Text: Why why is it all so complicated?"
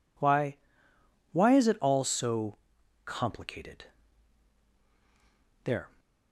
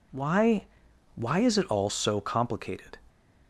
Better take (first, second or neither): second